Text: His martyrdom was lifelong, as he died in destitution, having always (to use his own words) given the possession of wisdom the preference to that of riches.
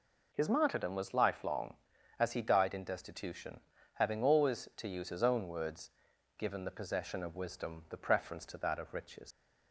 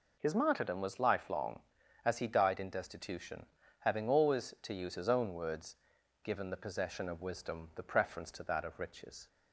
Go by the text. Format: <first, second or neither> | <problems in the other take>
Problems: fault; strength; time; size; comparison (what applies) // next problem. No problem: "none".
second | leaves "riches" unfinished; at 9.3 s; 115 ms